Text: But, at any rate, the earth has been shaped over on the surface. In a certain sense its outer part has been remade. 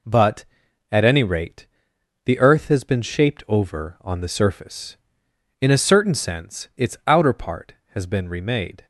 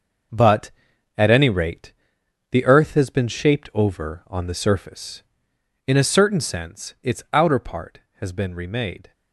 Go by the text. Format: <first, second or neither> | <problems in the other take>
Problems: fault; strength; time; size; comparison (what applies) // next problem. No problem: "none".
first | gets quieter; strong; throughout; 10 dB